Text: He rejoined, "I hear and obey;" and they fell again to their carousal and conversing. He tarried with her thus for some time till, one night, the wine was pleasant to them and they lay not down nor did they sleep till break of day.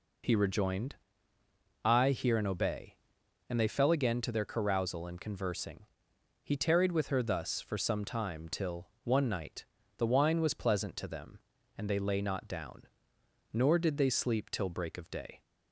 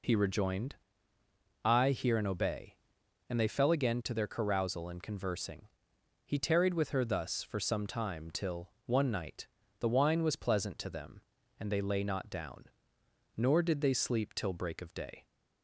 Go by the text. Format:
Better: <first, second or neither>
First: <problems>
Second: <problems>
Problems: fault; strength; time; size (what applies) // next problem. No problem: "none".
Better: neither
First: pauses between "down" and "nor"; noticeable; at 12.8 s; 0.64 s long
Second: pauses between "down" and "nor"; noticeable; at 12.6 s; 0.66 s long